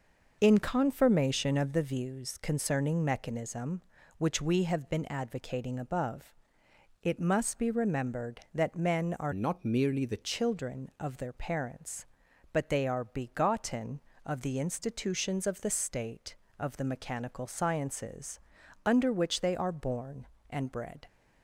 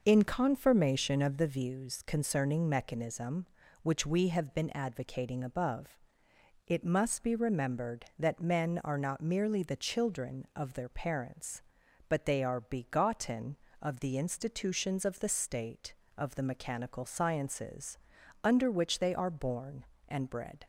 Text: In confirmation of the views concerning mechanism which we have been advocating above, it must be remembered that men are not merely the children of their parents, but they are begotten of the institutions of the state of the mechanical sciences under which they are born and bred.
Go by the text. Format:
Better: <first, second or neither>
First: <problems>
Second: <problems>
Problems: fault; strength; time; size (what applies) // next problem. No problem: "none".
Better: second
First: changes voice from "not" to "the"; from 9.3 to 10.2 s; 0.9 s long // pauses between "sciences" and "under"; at 18.4 s; 0.44 s long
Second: pauses between "sciences" and "under"; at 17.9 s; 0.44 s long